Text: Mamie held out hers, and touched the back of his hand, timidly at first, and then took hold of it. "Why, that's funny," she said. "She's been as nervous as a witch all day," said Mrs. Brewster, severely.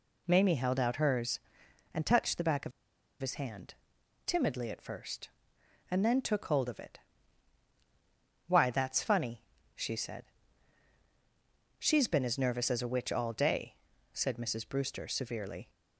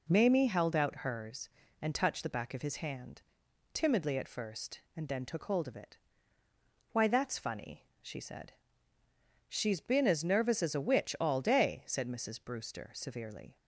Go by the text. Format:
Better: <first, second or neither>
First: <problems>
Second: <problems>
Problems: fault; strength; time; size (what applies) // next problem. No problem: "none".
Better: second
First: pauses between "of" and "his"; noticeable; at 2.7 s; 0.50 s long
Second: none